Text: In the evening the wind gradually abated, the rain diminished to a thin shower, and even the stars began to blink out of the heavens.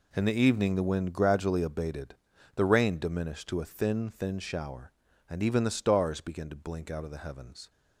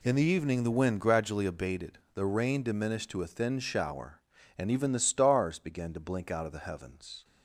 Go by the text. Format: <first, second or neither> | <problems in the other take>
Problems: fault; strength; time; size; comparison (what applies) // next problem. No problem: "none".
second | says "thin" twice; at 4.0 s